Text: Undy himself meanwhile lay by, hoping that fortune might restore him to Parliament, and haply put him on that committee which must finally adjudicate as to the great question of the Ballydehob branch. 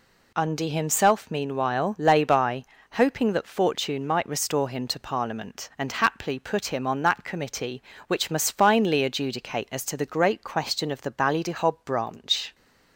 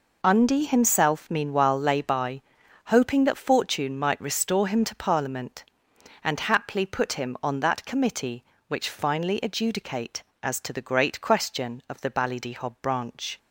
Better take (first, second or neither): first